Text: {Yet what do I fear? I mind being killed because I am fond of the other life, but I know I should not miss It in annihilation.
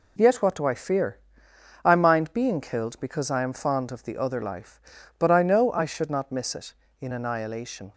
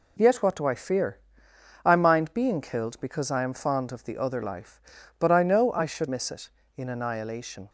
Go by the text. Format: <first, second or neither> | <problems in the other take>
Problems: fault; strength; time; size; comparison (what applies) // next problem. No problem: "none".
first | skips "not"; at 6.0 s